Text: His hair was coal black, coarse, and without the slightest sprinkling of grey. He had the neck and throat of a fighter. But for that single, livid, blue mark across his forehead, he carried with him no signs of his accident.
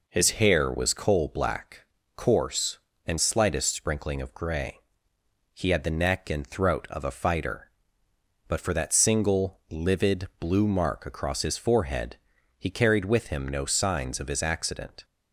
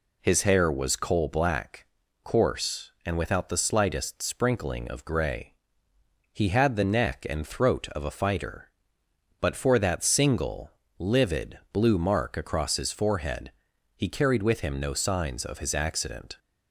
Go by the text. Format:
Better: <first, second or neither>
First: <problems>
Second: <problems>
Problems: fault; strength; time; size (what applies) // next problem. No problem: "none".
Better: second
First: skips "without the"; at 3.1 s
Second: none